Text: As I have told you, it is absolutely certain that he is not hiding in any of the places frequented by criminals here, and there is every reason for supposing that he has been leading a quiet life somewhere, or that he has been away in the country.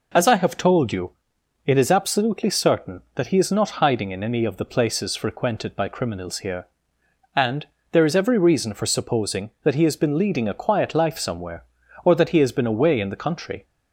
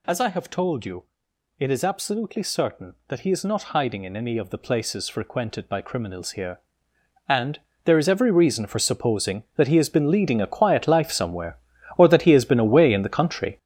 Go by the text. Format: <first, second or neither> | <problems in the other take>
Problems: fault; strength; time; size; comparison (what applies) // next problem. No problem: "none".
first | gets louder; strong; throughout; 9 dB // pauses between "and" and "there"; slight; at 7.5 s; 0.28 s long; slight in the first